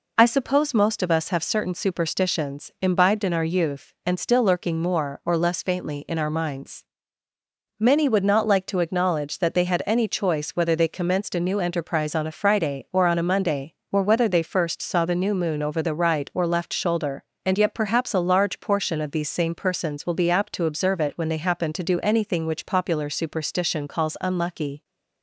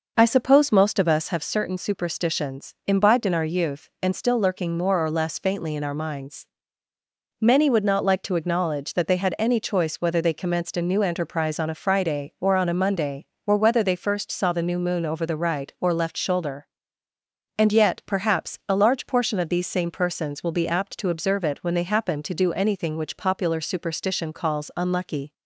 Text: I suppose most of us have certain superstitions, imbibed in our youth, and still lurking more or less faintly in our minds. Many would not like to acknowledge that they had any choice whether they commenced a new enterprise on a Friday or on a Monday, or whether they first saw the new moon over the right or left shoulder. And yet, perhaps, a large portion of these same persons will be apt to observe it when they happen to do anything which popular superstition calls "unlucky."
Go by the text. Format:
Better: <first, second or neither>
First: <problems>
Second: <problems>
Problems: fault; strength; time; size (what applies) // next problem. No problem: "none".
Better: first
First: none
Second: starts louder than the rest; noticeable; until 1.4 s; 5.5 dB